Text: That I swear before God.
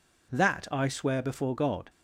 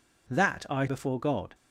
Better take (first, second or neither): first